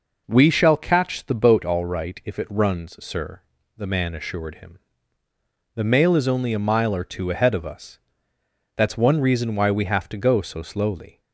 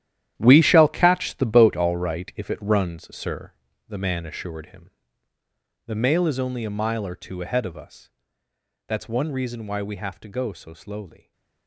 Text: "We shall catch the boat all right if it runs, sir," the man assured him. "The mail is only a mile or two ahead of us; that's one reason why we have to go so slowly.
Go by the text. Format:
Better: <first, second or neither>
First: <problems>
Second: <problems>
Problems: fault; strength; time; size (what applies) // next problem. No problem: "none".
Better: first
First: none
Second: gets quieter; strong; throughout; 13 dB // stays silent after the last word; slight; from 11.1 s on; 0.5 s long